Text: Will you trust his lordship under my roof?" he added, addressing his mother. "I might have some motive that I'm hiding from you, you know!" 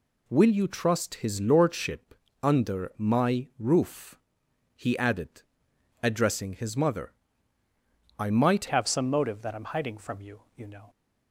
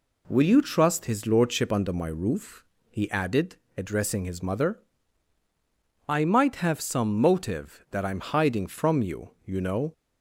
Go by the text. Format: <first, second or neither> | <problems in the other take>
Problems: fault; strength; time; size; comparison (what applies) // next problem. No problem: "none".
second | pauses between "lordship" and "under"; slight; at 2.1 s; 0.30 s long // changes voice at "have"; from 8.6 s on; 2.2 s long